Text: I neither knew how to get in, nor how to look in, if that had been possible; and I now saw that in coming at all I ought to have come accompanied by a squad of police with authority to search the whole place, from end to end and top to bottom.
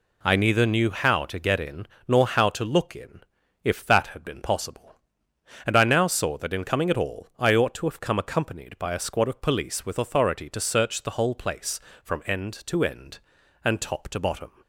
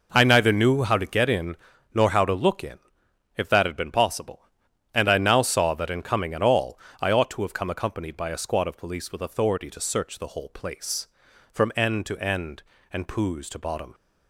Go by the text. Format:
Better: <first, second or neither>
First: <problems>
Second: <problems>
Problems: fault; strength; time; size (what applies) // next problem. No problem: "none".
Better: first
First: none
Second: pauses between "all" and "I"; slight; at 6.7 s; 0.24 s long // says "poos" for "top"; at 13.0 s